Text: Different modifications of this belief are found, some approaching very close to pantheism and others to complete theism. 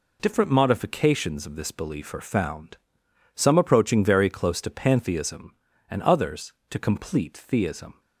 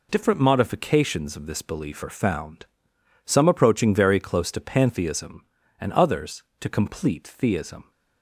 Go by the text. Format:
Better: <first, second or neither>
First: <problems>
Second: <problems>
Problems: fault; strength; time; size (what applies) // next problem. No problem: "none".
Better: neither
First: none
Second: none